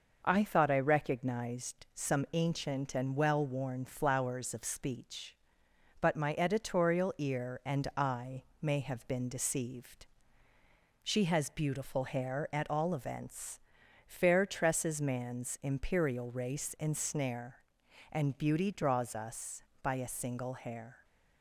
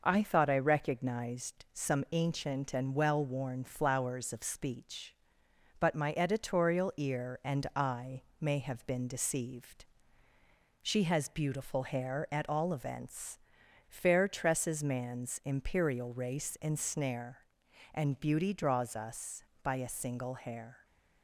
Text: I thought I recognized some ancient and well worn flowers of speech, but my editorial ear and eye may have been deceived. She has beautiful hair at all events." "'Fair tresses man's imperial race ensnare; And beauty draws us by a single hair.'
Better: neither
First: pauses between "eye" and "may"; slight; at 8.4 s; 0.16 s long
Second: pauses between "eye" and "may"; slight; at 8.2 s; 0.16 s long

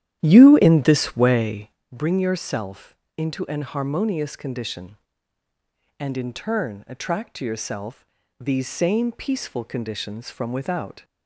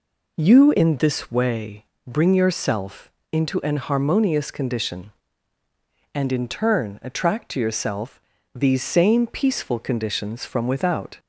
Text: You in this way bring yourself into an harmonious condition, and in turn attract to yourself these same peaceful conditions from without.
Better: second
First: starts louder than the rest; strong; until 1.8 s; 11.5 dB // pauses between "way" and "bring"; slight; at 1.7 s; 0.22 s long // pauses between "yourself" and "into"; slight; at 2.9 s; 0.20 s long // pauses between "yourself" and "these"; slight; at 8.0 s; 0.36 s long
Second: pauses between "way" and "bring"; slight; at 1.8 s; 0.22 s long // pauses between "yourself" and "into"; slight; at 3.1 s; 0.20 s long // pauses between "yourself" and "these"; slight; at 8.1 s; 0.36 s long

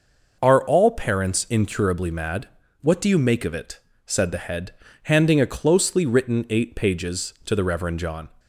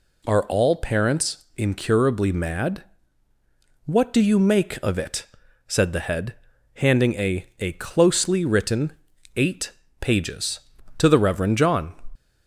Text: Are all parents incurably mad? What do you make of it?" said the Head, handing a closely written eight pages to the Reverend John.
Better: first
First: none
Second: says "a" twice; at 7.5 s // pauses between "written" and "eight"; at 8.9 s; 0.44 s long // pauses between "eight" and "pages"; slight; at 9.7 s; 0.28 s long

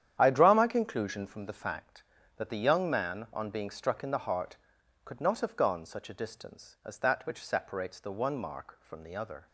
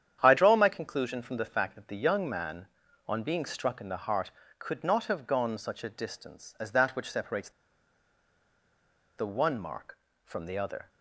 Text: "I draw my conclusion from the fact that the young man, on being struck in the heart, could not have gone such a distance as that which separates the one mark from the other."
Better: first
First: starts louder than the rest; strong; until 1.2 s; 10 dB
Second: starts louder than the rest; strong; until 1.2 s; 9 dB // pauses between "separates" and "the"; strong; at 7.4 s; 1.6 s long

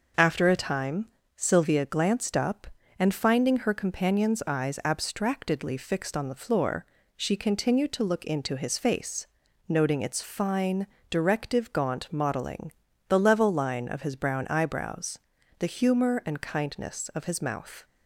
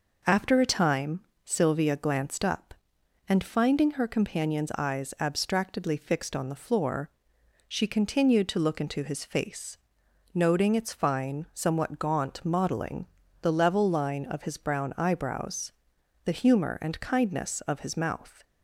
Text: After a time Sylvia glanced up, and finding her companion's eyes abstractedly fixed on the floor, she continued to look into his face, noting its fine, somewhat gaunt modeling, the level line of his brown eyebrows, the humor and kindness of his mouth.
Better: second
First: pauses between "time" and "Sylvia"; slight; at 1.0 s; 0.30 s long // says "directive" for "somewhat"; at 11.1 s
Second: pauses between "time" and "Sylvia"; slight; at 1.1 s; 0.24 s long

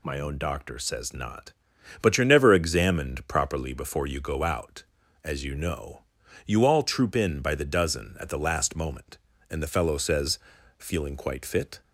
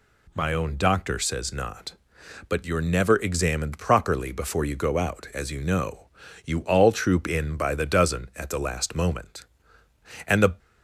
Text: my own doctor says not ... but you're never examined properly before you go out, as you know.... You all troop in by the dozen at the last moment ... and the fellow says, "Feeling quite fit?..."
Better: first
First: none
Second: stops before "fellow says Feeling quite fit"; at 10.5 s

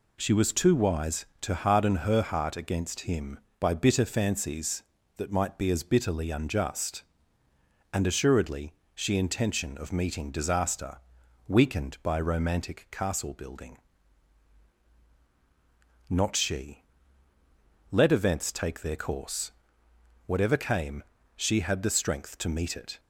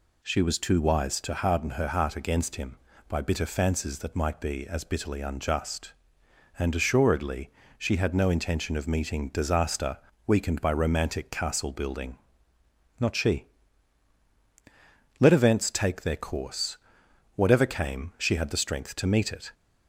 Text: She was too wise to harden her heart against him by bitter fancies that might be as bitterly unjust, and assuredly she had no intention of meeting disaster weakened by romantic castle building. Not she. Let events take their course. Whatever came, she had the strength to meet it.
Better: second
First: pauses between "assuredly" and "she"; slight; at 8.7 s; 0.20 s long // skips "had no"; at 9.1 s // pauses between "disaster" and "weakened"; noticeable; at 10.9 s; 0.50 s long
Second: pauses between "assuredly" and "she"; slight; at 7.5 s; 0.26 s long // pauses between "disaster" and "weakened"; slight; at 9.9 s; 0.28 s long

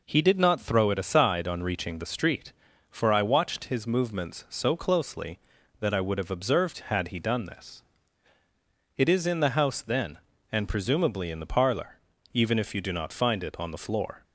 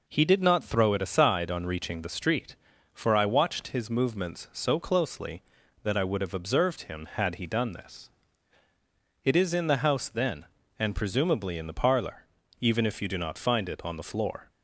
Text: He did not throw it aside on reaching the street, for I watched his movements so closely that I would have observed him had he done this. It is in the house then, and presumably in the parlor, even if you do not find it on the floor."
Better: second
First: skips "him"; at 6.8 s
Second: none

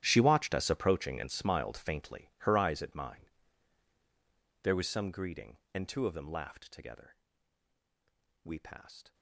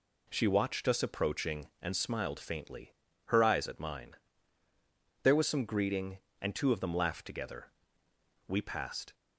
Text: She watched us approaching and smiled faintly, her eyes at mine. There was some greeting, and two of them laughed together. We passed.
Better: second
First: gets quieter; strong; throughout; 19 dB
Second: none

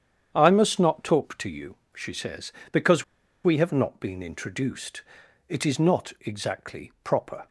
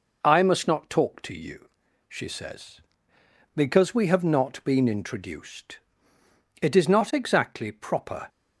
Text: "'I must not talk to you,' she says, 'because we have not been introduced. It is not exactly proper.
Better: second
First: starts louder than the rest; strong; until 1.3 s; 8.5 dB // pauses between "because" and "we"; at 3.0 s; 0.41 s long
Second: none

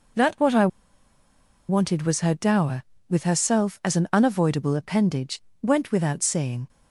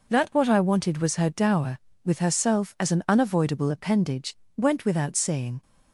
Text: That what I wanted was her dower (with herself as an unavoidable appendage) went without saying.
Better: second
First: pauses between "I" and "wanted"; at 0.6 s; 1.0 s long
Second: none

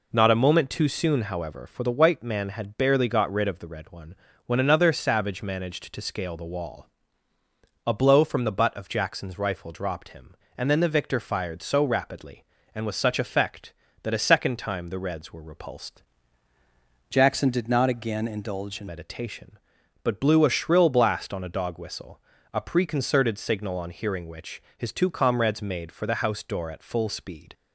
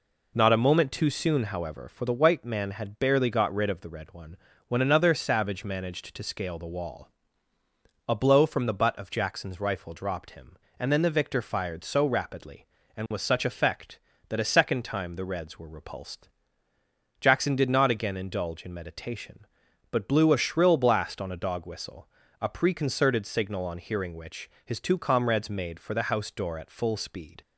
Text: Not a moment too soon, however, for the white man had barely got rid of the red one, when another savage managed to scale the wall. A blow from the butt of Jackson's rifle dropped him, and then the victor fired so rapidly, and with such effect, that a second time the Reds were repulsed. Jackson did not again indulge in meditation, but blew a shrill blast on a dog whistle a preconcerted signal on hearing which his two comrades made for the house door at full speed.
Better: second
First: changes voice from "Jackson" to "in"; from 17.0 to 18.8 s; 1.8 s long // pauses between "whistle" and "a"; slight; at 22.1 s; 0.32 s long // pauses between "which" and "his"; slight; at 24.5 s; 0.16 s long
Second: pauses between "whistle" and "a"; slight; at 22.0 s; 0.32 s long // pauses between "which" and "his"; slight; at 24.4 s; 0.16 s long

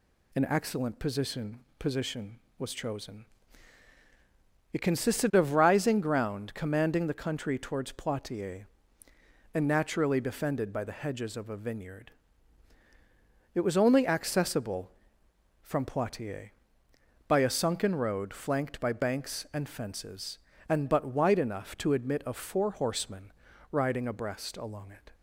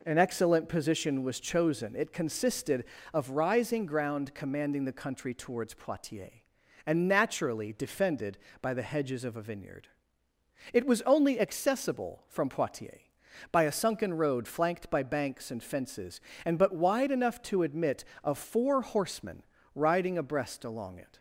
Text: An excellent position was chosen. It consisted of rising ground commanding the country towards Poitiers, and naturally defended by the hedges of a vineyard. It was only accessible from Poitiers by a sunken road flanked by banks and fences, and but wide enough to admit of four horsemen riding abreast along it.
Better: second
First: says "position" twice; at 1.7 s // pauses between "horsemen" and "riding"; at 23.3 s; 0.40 s long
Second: pauses between "horsemen" and "riding"; slight; at 19.4 s; 0.32 s long

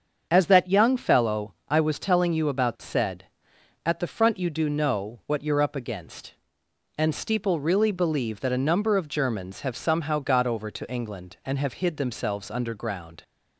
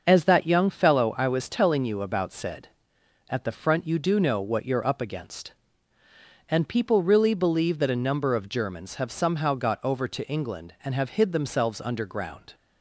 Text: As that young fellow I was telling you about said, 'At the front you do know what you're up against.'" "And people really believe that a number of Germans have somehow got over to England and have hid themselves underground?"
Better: second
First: starts louder than the rest; strong; until 1.3 s; 7 dB // pauses between "fellow" and "I"; slight; at 1.5 s; 0.16 s long // says "steeple" for "people"; at 7.1 s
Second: starts louder than the rest; until 1.0 s; 6.5 dB

